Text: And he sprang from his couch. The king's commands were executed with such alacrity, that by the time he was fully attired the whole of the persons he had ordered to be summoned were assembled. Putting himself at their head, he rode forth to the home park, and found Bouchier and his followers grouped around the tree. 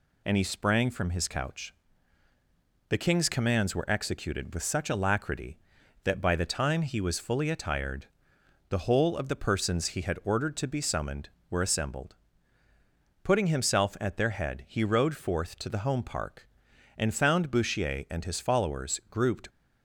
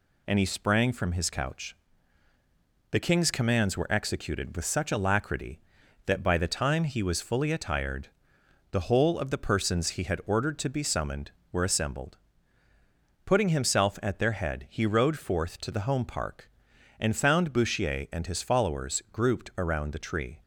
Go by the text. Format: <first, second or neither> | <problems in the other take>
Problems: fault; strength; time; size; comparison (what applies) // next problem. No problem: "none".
second | pauses between "attired" and "the"; noticeable; at 8.0 s; 0.64 s long; noticeable in the second // stops before "around the tree"; at 19.4 s